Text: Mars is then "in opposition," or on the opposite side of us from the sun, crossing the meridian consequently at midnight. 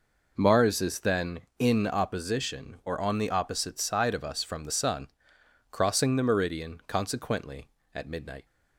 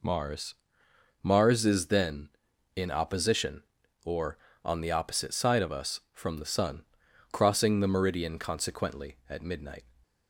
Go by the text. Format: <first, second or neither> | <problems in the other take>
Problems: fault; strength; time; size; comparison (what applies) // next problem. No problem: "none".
first | says "Mars" twice; at 1.2 s